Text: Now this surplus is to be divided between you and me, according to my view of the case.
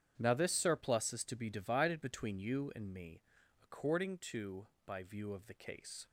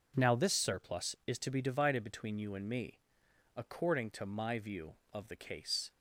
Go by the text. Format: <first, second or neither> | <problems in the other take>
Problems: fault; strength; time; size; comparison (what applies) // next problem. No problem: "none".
second | starts louder than the rest; strong; until 1.1 s; 9 dB // says "by" for "my"; at 4.8 s